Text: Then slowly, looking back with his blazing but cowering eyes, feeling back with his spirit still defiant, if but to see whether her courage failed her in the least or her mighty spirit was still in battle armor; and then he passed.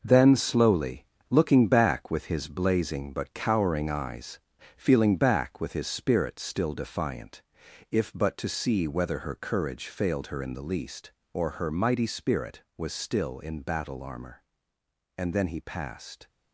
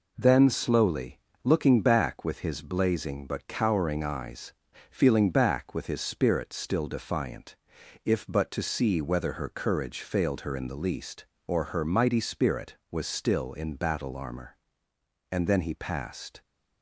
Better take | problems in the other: second | gets quieter; strong; throughout; 8.5 dB

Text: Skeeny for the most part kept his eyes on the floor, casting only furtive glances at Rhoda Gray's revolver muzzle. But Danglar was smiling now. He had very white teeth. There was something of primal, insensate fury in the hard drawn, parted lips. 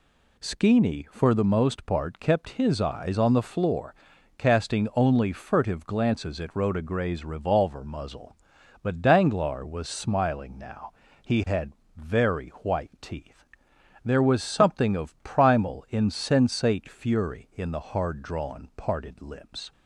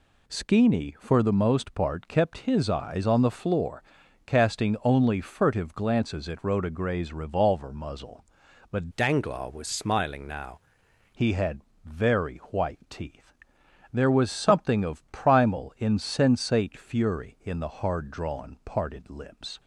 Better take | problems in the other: first | changes voice from "Danglar" to "now"; from 8.9 to 10.5 s; 1.6 s long // pauses between "had" and "very"; slight; at 11.6 s; 0.24 s long; slight in the first

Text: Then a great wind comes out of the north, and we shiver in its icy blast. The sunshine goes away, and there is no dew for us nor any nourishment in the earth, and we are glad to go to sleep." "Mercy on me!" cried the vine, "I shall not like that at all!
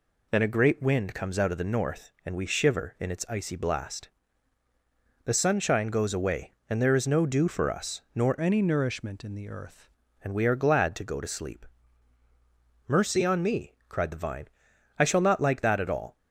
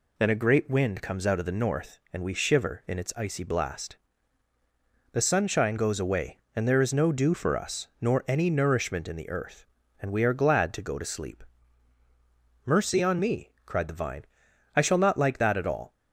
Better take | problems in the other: second | changes voice from "any" to "earth"; from 8.4 to 9.8 s; 1.4 s long

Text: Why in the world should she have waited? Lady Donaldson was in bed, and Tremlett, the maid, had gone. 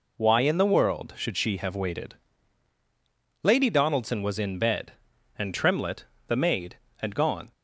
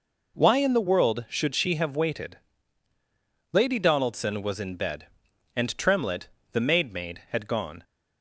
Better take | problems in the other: first | says "maid" twice; at 6.9 s

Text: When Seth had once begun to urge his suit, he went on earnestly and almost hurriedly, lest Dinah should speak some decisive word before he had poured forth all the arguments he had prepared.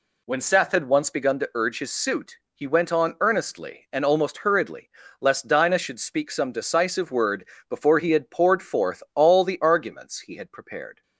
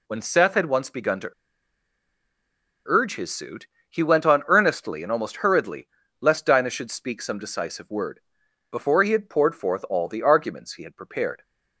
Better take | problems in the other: first | pauses between "to" and "urge"; strong; at 1.3 s; 1.5 s long // pauses between "word" and "before"; noticeable; at 8.2 s; 0.50 s long; slight in the first

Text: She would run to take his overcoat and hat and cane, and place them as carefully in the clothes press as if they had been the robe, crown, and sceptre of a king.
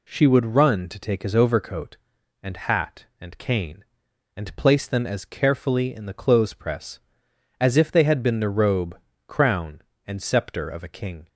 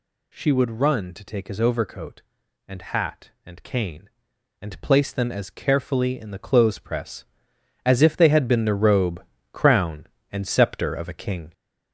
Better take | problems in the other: first | gets louder; noticeable; throughout; 4 dB

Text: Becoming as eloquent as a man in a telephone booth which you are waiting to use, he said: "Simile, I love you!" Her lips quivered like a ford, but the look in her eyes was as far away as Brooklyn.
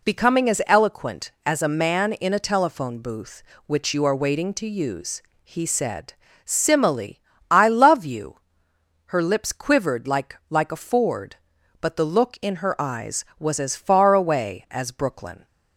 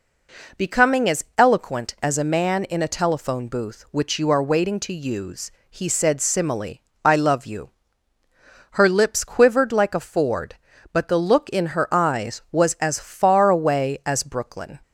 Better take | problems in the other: second | says "like" twice; at 10.4 s

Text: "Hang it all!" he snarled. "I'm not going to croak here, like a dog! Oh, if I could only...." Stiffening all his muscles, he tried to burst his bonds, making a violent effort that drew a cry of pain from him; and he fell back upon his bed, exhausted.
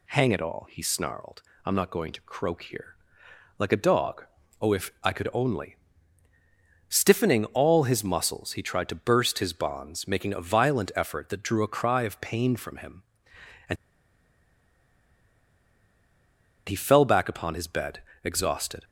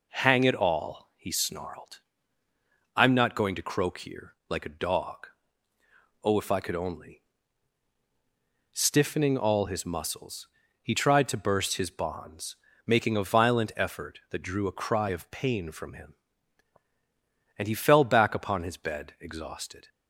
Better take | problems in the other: second | pauses between "and" and "he"; strong; at 13.7 s; 2.9 s long

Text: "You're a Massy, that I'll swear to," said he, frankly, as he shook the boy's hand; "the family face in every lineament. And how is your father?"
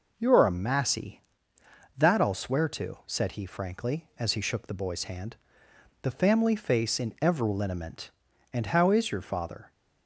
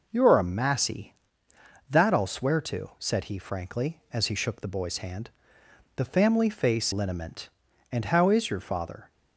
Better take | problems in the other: first | skips "in every"; at 6.9 s

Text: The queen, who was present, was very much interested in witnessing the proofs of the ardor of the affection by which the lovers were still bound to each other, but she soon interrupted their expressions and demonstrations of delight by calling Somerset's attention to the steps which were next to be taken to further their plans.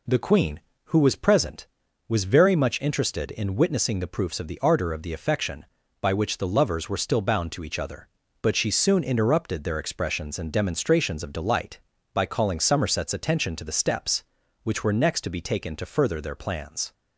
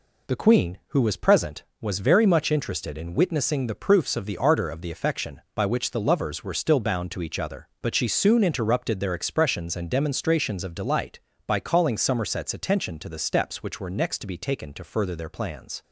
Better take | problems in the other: neither | none

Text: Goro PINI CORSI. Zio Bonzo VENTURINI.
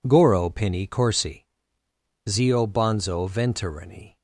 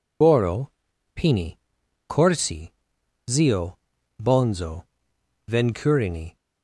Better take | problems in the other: first | loses the start of "Goro"; at 0.2 s; 65 ms // pauses between "Goro" and "PINI"; noticeable; at 0.6 s; 0.46 s long // pauses between "PINI" and "CORSI"; noticeable; at 1.5 s; 0.54 s long // pauses between "Zio" and "Bonzo"; at 3.7 s; 0.44 s long // pauses between "Bonzo" and "VENTURINI"; noticeable; at 4.8 s; 0.64 s long

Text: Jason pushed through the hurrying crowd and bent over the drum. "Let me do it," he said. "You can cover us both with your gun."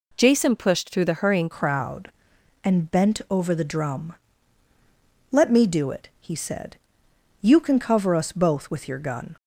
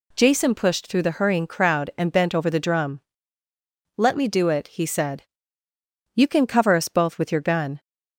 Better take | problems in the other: second | changes voice at "crowd"; from 1.5 s on; 7.8 s long

